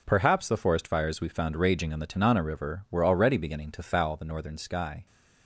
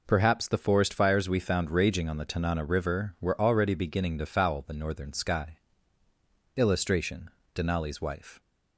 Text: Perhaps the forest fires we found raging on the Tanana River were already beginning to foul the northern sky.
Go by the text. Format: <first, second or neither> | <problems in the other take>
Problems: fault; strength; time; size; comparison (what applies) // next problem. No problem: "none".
first | goes on to say "Illustration Denali's Wife"; strong; from 6.5 s on; 1.8 s long